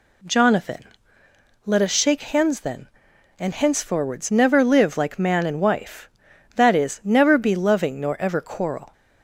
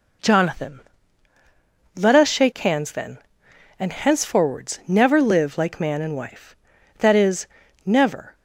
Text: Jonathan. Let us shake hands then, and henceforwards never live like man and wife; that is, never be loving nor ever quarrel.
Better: first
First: none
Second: stops before "be loving nor ever quarrel"; at 8.3 s

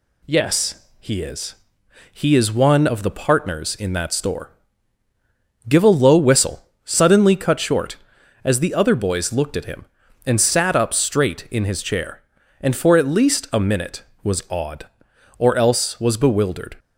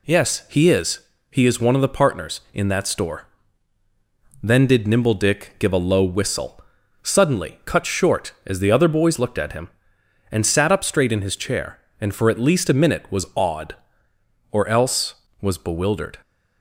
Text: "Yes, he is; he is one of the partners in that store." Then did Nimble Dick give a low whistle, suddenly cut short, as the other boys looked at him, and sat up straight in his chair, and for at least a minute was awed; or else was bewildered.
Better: second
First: skips "Then did Nimble Dick"; at 5.0 s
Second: none

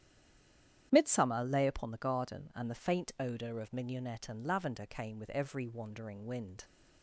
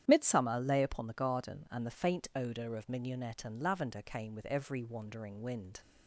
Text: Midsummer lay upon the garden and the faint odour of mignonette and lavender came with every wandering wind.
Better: second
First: stays silent before the first word; slight; until 0.9 s; 0.9 s long // starts louder than the rest; strong; until 1.9 s; 10 dB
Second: starts louder than the rest; strong; until 1.0 s; 10 dB

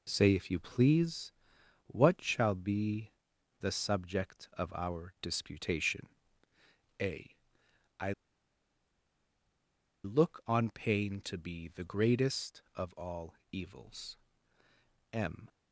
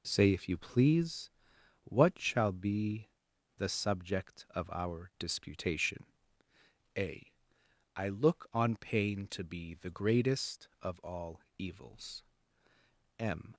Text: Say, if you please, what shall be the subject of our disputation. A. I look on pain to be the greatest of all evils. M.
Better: second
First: pauses between "be" and "the"; noticeable; at 3.0 s; 0.50 s long // pauses between "I" and "look"; strong; at 8.1 s; 1.9 s long // pauses between "all" and "evils"; slight; at 13.3 s; 0.16 s long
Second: pauses between "be" and "the"; noticeable; at 3.0 s; 0.50 s long // pauses between "all" and "evils"; slight; at 11.4 s; 0.16 s long

